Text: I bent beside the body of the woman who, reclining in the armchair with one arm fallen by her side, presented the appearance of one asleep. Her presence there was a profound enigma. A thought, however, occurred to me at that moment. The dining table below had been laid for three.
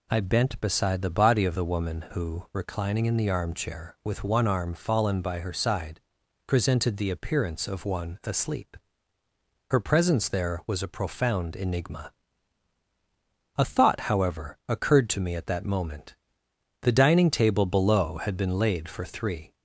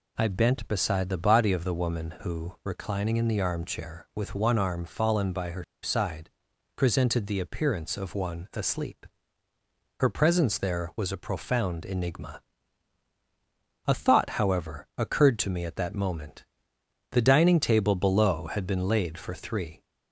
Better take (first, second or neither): first